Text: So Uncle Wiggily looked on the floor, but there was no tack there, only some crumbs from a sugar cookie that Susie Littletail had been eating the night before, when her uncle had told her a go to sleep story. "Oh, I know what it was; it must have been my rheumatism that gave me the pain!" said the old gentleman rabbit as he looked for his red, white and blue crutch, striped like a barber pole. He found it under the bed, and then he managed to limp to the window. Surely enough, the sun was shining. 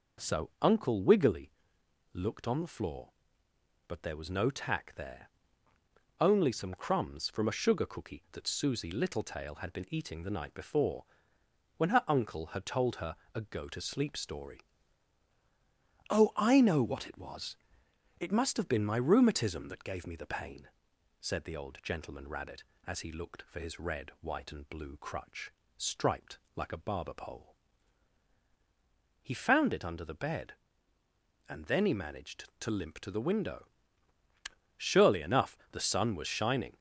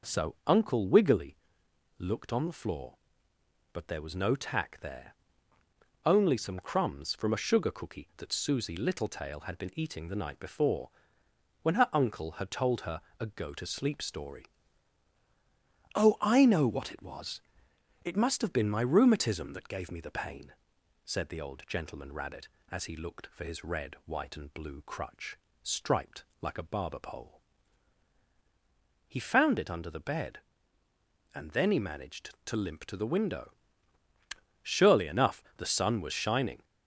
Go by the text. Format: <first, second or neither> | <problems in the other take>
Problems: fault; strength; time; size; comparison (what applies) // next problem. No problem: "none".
neither | pauses between "Wiggily" and "looked"; noticeable; the same in both // pauses between "her" and "a"; slight; the same in both // pauses between "striped" and "like"; slight; the same in both